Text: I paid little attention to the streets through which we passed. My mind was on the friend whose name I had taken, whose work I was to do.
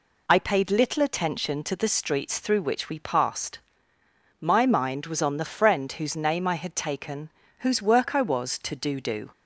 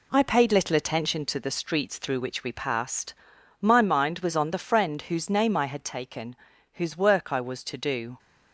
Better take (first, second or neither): second